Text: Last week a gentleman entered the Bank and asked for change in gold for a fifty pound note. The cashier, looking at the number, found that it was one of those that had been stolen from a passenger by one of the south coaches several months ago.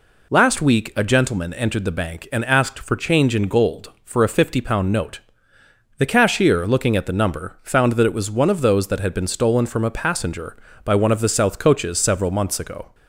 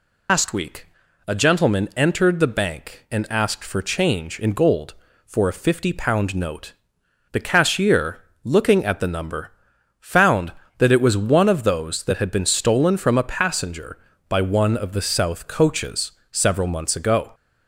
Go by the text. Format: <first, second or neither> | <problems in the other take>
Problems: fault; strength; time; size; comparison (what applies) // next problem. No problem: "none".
first | loses the start of "Last"; at 0.2 s; 140 ms // pauses between "week" and "a"; at 0.8 s; 0.42 s long // pauses between "coaches" and "several"; slight; at 16.1 s; 0.20 s long